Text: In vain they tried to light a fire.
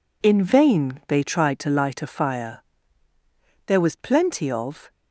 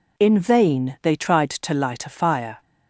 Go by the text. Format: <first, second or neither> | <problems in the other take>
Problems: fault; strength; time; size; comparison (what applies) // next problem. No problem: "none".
second | goes on to say "There was plenty of"; noticeable; from 3.6 s on; 1.2 s long